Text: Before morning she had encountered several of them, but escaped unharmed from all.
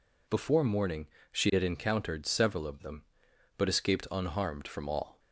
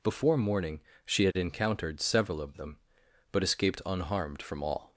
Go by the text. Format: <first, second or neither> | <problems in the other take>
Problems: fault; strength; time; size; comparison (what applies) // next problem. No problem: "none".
neither | pauses between "morning" and "she"; slight; the same in both